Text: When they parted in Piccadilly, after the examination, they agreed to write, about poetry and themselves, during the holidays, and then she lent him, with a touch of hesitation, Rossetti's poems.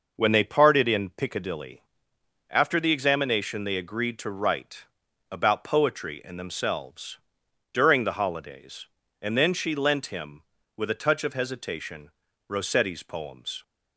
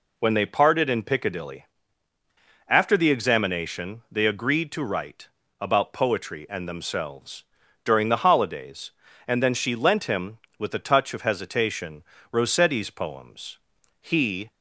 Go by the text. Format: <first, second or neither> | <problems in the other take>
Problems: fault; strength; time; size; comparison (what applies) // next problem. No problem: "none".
first | goes on to say "He"; from 13.9 s on; 0.50 s long